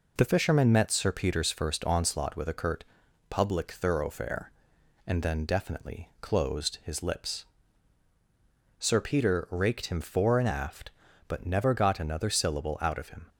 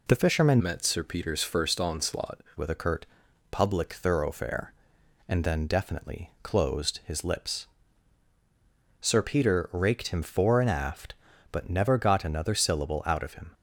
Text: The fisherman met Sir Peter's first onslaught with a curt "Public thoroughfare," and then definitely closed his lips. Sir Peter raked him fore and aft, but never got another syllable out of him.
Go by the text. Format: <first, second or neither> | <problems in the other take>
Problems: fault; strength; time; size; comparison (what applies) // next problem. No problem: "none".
first | changes voice from "met" to "onslaught"; from 0.6 to 2.4 s; 1.8 s long // pauses between "curt" and "Public"; at 3.0 s; 0.44 s long; also in the first